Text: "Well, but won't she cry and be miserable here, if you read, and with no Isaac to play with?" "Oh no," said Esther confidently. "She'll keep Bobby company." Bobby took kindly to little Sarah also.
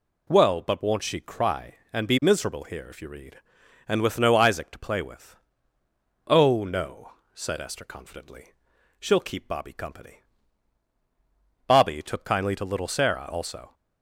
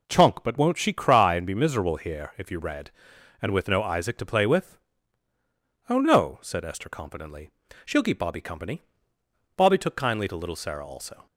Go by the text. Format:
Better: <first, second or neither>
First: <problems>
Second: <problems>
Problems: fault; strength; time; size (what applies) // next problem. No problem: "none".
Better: first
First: none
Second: says "Chunk" for "Well"; at 0.0 s